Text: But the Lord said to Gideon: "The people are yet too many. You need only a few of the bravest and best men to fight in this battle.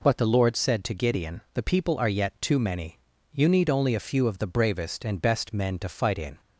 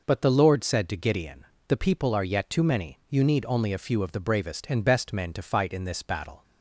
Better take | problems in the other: second | stops before "this battle"; at 6.4 s

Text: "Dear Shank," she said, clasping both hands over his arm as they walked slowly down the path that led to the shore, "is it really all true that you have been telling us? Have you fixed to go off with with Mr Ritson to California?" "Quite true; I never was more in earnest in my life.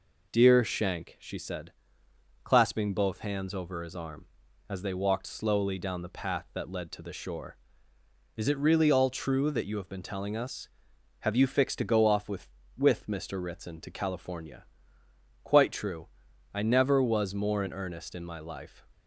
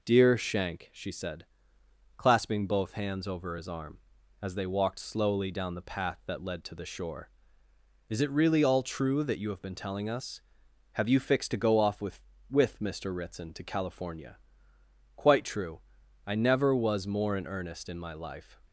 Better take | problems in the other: neither | none

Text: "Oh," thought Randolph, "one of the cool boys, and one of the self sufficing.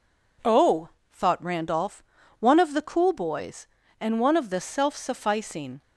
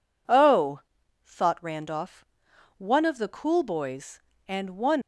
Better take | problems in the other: first | stops before "of the self sufficing"; at 5.0 s

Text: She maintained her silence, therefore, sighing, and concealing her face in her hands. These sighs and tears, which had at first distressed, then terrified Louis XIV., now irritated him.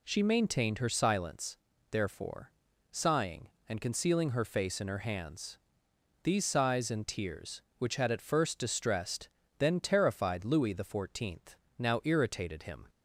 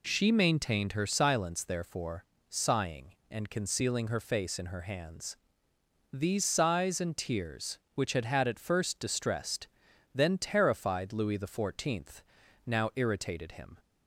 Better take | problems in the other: first | says "had" twice; at 8.2 s

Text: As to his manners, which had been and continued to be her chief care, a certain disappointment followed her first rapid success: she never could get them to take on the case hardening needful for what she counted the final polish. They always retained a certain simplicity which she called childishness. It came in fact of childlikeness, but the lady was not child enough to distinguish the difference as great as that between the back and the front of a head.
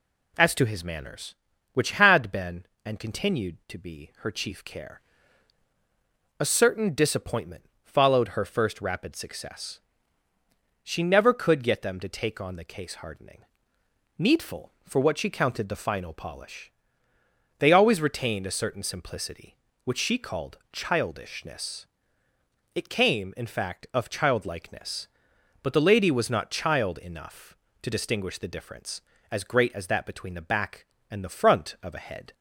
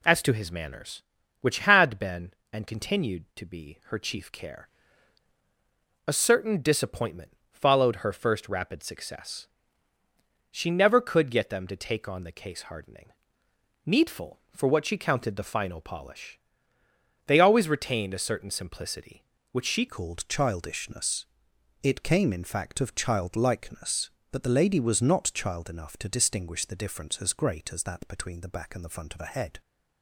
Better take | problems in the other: first | pauses between "disappointment" and "followed"; slight; at 7.2 s; 0.22 s long; slight in the first // pauses between "hardening" and "needful"; noticeable; at 13.1 s; 0.74 s long; noticeable in the first // changes voice at "called"; from 19.8 s on; 9.7 s long

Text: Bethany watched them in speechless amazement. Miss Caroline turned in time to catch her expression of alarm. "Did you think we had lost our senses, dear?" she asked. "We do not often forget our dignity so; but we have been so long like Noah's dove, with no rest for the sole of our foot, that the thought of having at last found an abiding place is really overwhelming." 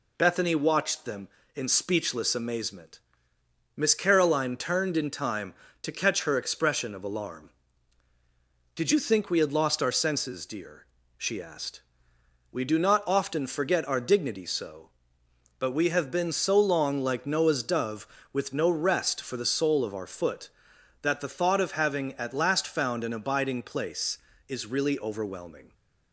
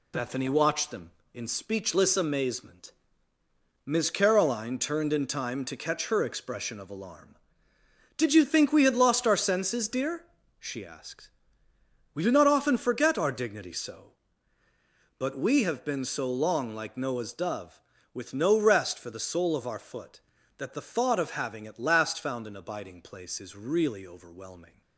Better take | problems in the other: first | gets quieter; throughout; 6.5 dB

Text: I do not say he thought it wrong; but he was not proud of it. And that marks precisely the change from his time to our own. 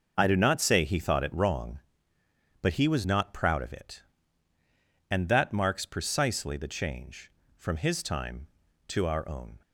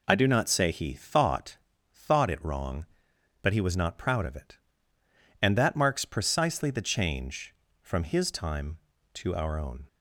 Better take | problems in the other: first | says "thought" twice; at 1.9 s

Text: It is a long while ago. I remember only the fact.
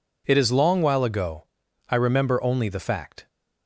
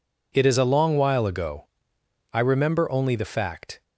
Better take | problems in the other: second | skips "a"; at 0.5 s

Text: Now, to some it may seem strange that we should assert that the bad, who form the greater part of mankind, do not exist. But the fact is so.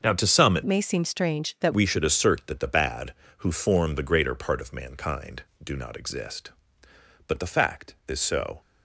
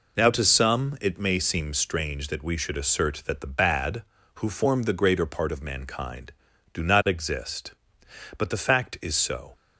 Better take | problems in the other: second | starts louder than the rest; until 1.0 s; 6.5 dB // changes voice from "may" to "that"; from 0.6 to 1.7 s; 1.1 s long

